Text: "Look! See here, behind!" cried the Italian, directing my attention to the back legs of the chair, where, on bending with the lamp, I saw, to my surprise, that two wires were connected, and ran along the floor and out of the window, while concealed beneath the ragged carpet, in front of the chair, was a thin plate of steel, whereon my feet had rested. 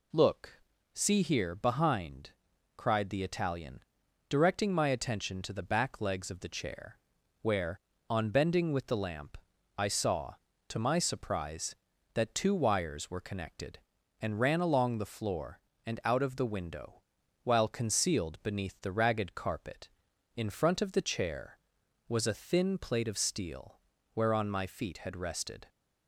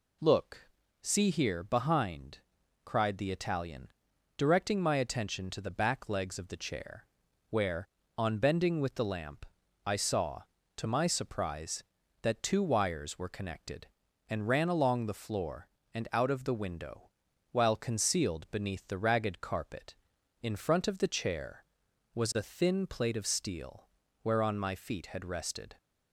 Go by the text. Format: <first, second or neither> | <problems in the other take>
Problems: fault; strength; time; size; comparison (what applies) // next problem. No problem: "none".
neither | none